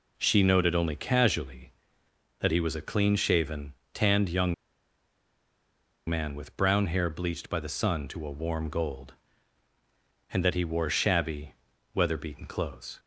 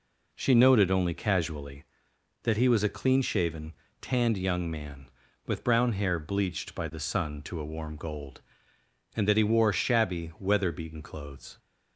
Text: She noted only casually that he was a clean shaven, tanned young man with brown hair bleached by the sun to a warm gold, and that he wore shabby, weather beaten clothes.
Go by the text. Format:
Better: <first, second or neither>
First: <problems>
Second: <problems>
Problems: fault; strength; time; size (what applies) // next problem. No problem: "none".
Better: second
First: pauses between "young" and "man"; strong; at 4.5 s; 1.5 s long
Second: none